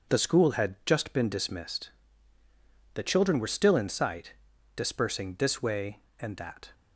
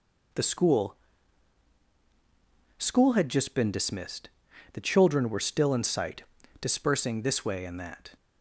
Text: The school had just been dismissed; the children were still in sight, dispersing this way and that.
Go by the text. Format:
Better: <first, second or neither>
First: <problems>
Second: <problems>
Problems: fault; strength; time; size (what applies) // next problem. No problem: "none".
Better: first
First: none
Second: says "school" twice; at 2.7 s